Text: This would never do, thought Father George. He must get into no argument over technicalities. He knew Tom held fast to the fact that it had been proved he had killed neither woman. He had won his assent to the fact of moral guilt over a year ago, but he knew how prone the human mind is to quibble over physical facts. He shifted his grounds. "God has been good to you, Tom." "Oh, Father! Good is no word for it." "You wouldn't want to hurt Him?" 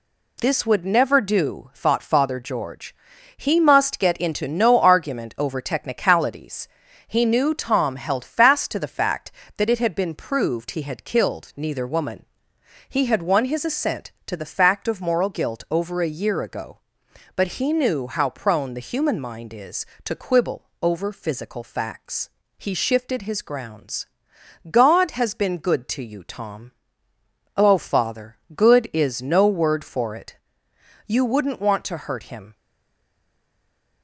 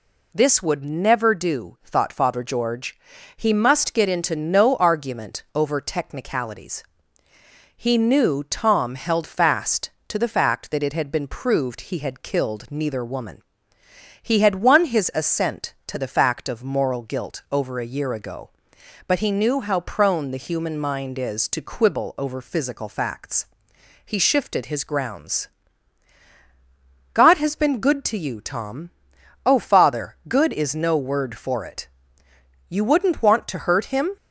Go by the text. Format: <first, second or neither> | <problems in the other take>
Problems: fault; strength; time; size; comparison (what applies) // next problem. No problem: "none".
second | stays silent after the last word; noticeable; from 32.5 s on; 1.5 s long